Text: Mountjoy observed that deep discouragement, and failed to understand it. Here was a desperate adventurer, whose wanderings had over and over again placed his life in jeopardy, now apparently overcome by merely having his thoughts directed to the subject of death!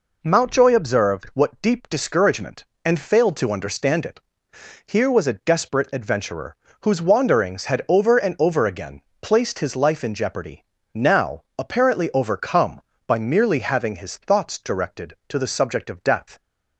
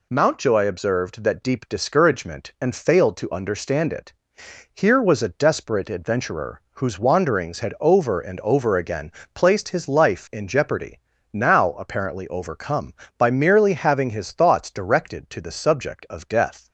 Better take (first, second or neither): second